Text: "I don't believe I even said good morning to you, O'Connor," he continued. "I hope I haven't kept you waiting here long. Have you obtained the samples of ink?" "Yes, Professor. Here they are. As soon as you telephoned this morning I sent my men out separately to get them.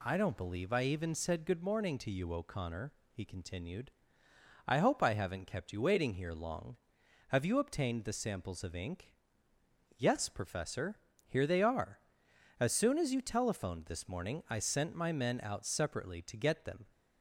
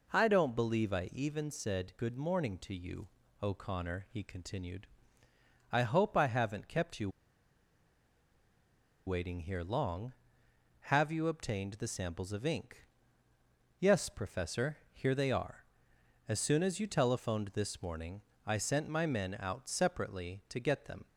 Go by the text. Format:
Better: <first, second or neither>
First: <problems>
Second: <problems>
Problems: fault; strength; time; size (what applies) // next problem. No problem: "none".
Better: first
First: none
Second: pauses between "you" and "waiting"; strong; at 7.1 s; 1.9 s long // pauses between "morning" and "I"; slight; at 18.2 s; 0.24 s long